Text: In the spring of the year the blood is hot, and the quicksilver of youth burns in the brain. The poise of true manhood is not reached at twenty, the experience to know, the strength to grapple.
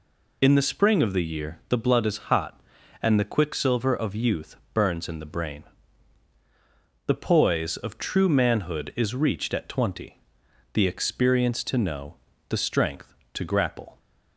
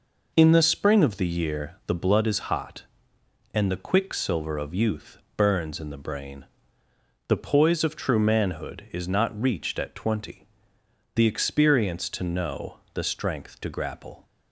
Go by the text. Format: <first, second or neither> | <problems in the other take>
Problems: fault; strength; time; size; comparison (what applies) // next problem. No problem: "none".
second | pauses between "youth" and "burns"; slight; at 4.5 s; 0.18 s long; slight in the second // skips "not"; at 9.1 s